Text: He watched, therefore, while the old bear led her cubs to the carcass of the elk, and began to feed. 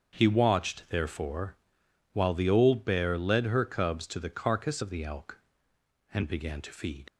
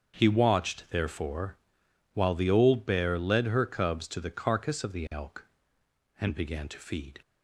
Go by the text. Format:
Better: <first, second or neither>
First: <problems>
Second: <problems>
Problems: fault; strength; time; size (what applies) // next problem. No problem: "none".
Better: second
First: starts louder than the rest; until 1.2 s; 7 dB // leaves "feed" unfinished; at 7.0 s; 45 ms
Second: starts louder than the rest; until 1.2 s; 7 dB